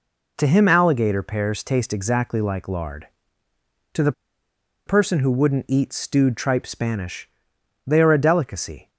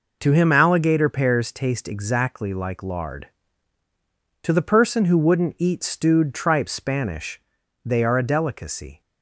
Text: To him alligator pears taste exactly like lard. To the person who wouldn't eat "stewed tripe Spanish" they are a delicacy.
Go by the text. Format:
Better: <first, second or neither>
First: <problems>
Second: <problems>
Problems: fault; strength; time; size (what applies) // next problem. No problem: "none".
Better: second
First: pauses between "the" and "person"; noticeable; at 4.1 s; 0.75 s long // pauses between "Spanish" and "they"; noticeable; at 7.2 s; 0.56 s long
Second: pauses between "Spanish" and "they"; at 7.4 s; 0.44 s long